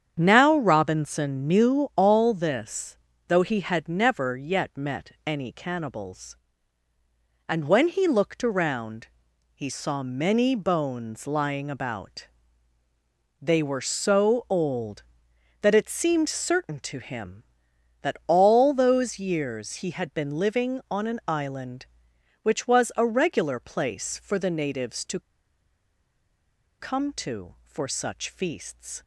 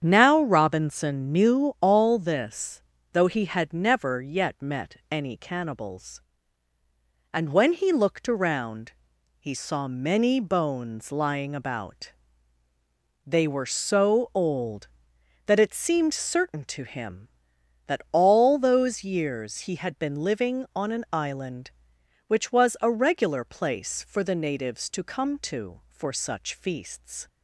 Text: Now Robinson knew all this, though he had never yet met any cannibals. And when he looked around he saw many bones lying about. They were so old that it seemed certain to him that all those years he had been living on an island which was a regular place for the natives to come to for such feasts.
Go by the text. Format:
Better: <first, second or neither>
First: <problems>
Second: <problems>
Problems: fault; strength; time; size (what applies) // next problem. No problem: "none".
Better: second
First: starts louder than the rest; strong; until 1.2 s; 8 dB // pauses between "around" and "he"; noticeable; at 9.0 s; 0.48 s long // pauses between "to" and "come"; strong; at 25.2 s; 1.5 s long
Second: starts louder than the rest; strong; until 1.0 s; 8 dB // pauses between "around" and "he"; noticeable; at 8.9 s; 0.48 s long